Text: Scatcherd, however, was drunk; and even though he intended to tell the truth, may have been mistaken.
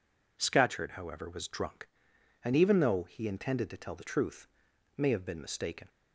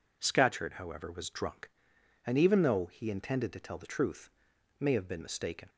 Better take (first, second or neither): neither